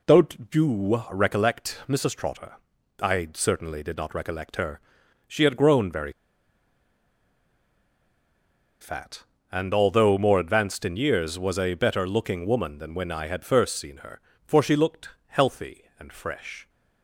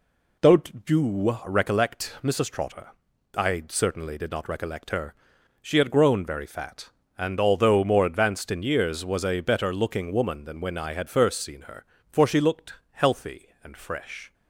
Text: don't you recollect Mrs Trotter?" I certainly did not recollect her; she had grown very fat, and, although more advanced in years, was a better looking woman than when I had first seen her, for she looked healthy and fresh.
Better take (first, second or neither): second